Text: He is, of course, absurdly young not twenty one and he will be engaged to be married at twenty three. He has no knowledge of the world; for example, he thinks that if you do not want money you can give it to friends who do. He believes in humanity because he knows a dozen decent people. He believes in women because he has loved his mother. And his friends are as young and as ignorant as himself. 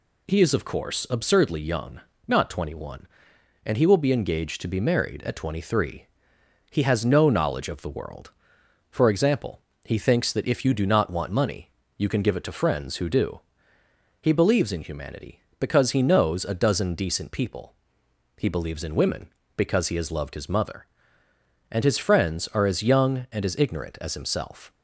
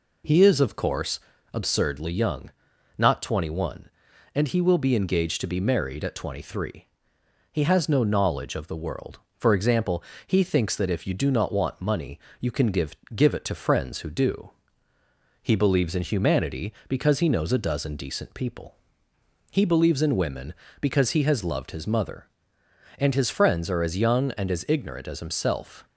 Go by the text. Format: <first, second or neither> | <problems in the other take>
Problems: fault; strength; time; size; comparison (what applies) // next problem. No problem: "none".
first | pauses between "young" and "not"; noticeable; at 2.4 s; 0.48 s long; slight in the first // pauses between "money" and "you"; slight; at 12.1 s; 0.22 s long; slight in the first // says "give" twice; at 13.1 s